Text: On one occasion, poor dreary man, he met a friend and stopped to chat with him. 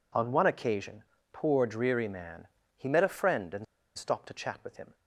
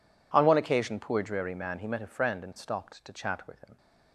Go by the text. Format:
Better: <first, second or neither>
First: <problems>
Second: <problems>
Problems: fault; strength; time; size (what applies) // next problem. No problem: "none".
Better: second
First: pauses between "and" and "stopped"; slight; at 3.6 s; 0.32 s long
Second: none